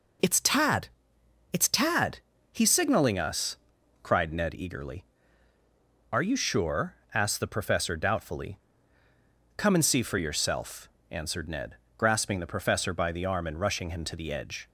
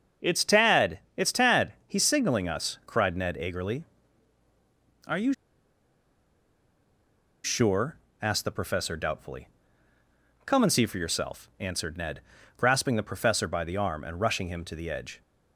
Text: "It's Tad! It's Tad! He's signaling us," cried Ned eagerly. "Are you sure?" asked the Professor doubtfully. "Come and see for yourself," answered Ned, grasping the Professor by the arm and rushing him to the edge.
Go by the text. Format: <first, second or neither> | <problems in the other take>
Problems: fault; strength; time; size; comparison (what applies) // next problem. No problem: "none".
first | starts louder than the rest; until 1.4 s; 6.5 dB // pauses between "you" and "sure"; strong; at 5.3 s; 2.1 s long